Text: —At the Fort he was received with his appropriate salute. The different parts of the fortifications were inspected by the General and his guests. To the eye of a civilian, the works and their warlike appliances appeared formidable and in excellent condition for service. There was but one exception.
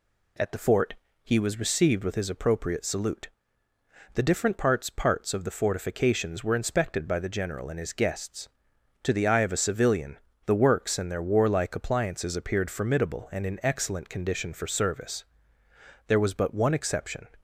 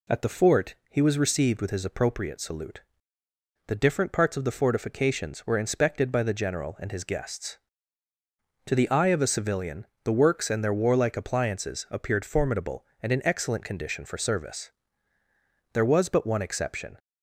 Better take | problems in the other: second | pauses between "Fort" and "he"; slight; at 0.9 s; 0.30 s long; slight in the second // says "parts" twice; at 4.8 s

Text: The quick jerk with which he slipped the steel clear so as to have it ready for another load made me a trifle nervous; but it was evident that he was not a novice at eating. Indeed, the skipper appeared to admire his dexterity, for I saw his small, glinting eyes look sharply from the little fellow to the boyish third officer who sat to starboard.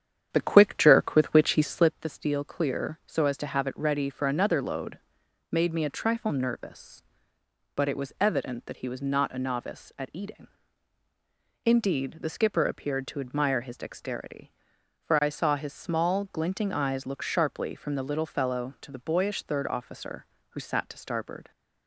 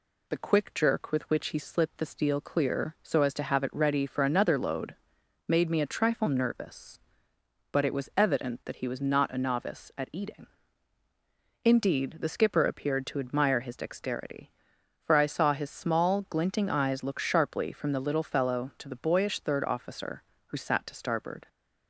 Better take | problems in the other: second | starts louder than the rest; strong; until 2.0 s; 8.5 dB // pauses between "load" and "made"; noticeable; at 4.9 s; 0.52 s long; noticeable in the second

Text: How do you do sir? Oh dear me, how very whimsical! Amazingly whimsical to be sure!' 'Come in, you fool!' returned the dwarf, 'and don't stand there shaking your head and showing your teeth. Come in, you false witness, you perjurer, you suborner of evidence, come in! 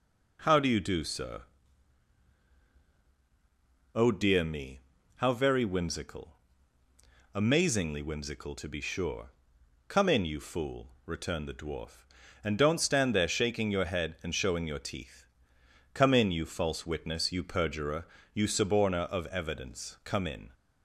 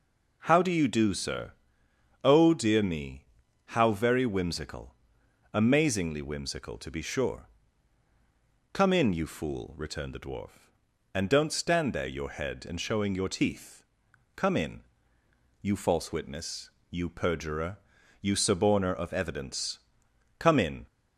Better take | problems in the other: first | skips "shaking"; at 12.0 s

